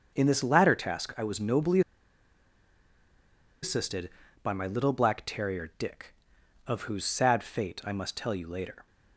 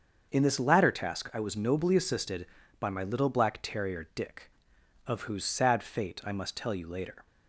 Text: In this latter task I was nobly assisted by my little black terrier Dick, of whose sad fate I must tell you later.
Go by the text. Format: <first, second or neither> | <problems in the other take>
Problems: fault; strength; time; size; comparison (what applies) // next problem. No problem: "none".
second | starts louder than the rest; until 1.1 s; 6.5 dB; also in the second // pauses between "nobly" and "assisted"; strong; at 1.8 s; 1.8 s long